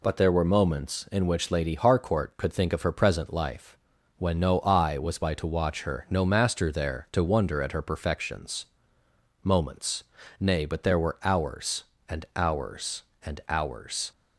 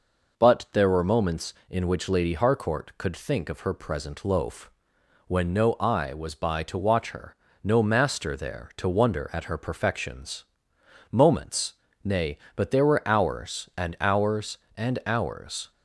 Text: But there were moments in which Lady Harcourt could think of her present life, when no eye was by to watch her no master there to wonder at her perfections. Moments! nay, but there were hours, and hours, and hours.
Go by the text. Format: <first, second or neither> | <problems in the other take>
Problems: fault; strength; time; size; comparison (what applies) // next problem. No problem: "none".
first | says "loaf" for "life"; at 4.2 s // pauses between "her" and "no"; slight; at 7.3 s; 0.32 s long